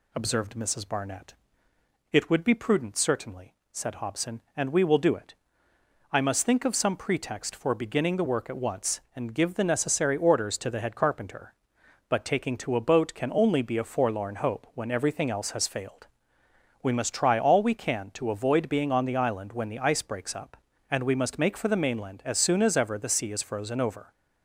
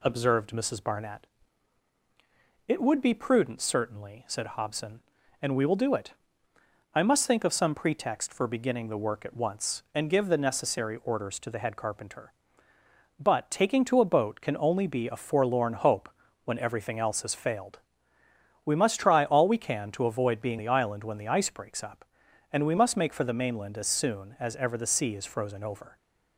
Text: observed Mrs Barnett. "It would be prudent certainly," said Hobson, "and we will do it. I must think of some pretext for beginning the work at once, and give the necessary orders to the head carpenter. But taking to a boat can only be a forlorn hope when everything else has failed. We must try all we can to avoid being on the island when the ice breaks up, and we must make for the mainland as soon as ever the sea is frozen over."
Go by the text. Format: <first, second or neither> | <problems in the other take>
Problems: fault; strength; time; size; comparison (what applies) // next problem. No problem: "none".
first | pauses between "hope" and "when"; slight; at 16.1 s; 0.34 s long // skips "on"; at 20.5 s